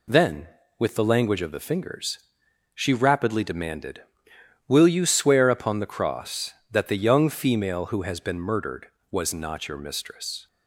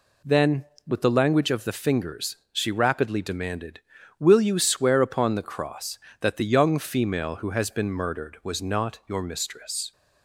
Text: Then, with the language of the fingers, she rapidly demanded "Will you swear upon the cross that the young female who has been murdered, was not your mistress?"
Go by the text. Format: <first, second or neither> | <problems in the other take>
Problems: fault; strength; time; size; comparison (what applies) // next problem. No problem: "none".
neither | none